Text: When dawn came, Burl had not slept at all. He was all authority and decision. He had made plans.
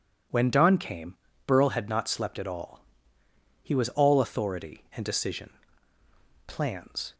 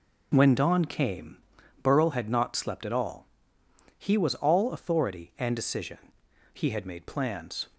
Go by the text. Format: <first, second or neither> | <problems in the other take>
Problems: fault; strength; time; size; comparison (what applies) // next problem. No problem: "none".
second | skips "He had made"; at 6.0 s